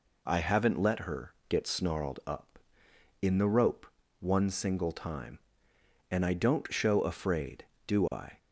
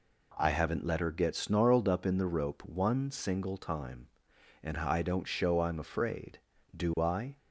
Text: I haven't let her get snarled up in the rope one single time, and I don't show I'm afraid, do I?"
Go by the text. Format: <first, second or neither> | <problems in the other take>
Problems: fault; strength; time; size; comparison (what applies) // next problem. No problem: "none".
second | pauses between "her" and "get"; slight; at 1.3 s; 0.16 s long // pauses between "rope" and "one"; slight; at 3.8 s; 0.34 s long // skips "I'm"; at 7.0 s